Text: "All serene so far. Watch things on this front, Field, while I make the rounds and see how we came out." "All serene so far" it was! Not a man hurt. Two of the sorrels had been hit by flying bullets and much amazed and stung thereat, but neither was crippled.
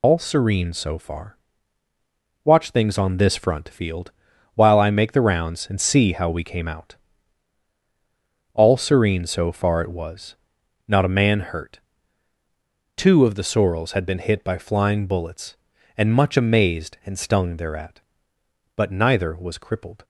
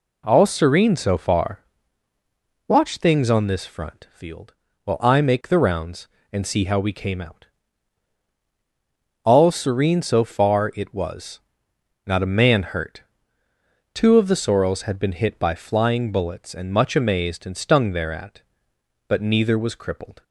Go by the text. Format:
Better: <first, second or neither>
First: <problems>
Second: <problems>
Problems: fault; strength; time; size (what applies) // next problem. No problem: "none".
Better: second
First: loses the start of "All"; at 0.0 s; 110 ms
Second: none